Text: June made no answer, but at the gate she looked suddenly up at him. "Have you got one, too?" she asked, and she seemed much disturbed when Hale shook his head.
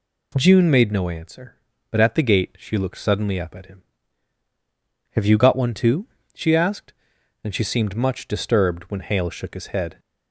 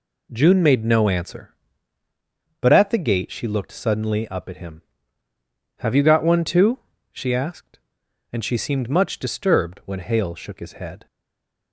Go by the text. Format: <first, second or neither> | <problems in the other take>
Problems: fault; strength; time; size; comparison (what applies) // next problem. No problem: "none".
first | stays silent after the last word; slight; from 11.0 s on; 0.7 s long